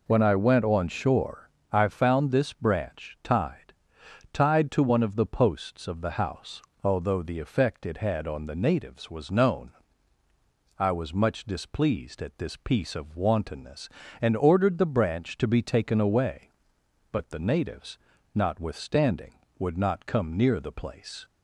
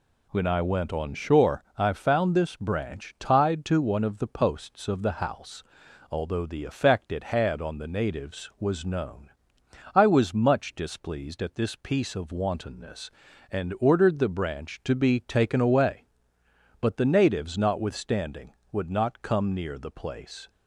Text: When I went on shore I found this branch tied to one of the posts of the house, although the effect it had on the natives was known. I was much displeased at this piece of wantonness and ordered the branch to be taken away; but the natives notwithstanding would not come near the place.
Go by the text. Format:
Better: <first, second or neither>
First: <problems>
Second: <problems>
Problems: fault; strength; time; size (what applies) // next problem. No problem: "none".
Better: second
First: pauses between "shore" and "I"; slight; at 1.4 s; 0.24 s long // says "tied" twice; at 4.3 s // pauses between "natives" and "notwithstanding"; at 17.9 s; 0.38 s long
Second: none